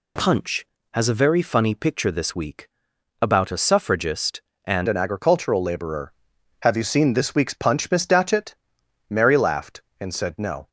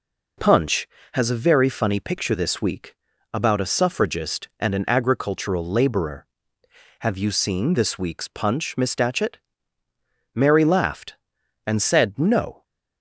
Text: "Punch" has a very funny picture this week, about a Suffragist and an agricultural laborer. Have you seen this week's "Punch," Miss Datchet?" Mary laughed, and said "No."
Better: second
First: changes voice at "an"; from 4.8 s on; 5.8 s long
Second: none

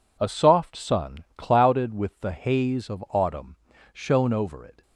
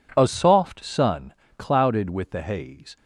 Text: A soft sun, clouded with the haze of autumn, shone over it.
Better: first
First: none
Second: stops before "of autumn shone over it"; at 2.9 s

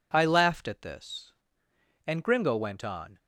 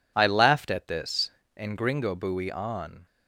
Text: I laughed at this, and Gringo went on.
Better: first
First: none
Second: says "buoy" for "went"; at 2.1 s

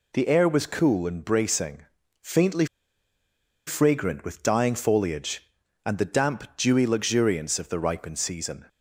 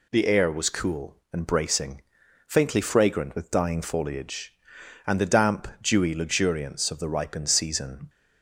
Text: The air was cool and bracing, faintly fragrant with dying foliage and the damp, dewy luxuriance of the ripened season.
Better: second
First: pauses between "faintly" and "fragrant"; at 2.6 s; 1.0 s long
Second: none

